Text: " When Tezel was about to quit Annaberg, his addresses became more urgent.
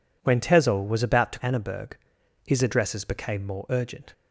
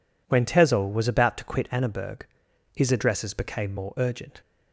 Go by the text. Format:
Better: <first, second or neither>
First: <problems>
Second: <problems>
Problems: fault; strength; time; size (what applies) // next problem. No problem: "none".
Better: second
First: skips "quit"; at 1.3 s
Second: none